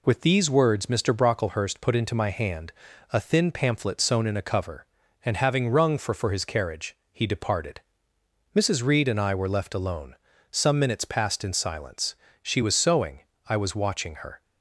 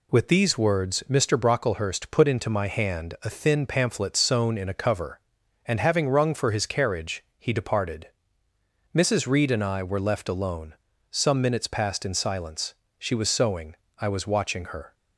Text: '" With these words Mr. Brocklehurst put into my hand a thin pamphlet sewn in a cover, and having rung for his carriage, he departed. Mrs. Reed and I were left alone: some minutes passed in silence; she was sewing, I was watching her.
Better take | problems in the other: second | pauses between "hand" and "a"; at 2.7 s; 0.38 s long // says "for" twice; at 6.1 s

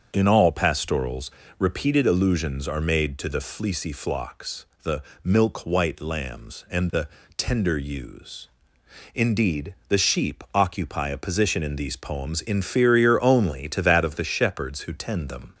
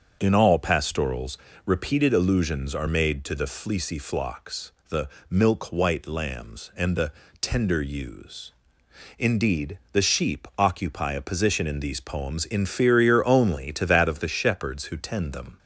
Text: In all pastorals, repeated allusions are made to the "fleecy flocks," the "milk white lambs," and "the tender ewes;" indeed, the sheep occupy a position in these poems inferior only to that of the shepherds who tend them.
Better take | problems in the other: neither | starts louder than the rest; the same in both // pauses between "the" and "milk"; slight; the same in both // pauses between "the" and "tender"; slight; the same in both

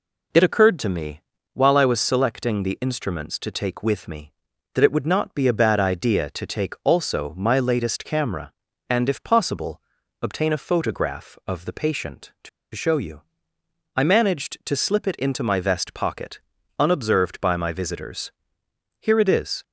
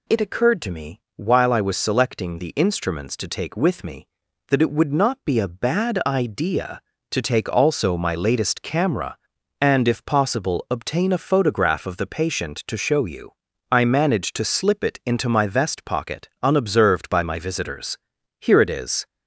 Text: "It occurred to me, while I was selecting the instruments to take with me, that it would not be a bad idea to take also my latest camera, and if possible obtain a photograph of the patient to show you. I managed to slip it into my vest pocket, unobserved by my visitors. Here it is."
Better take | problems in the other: second | pauses between "possible" and "obtain"; at 9.8 s; 0.42 s long // pauses between "to" and "show"; slight; at 12.4 s; 0.25 s long

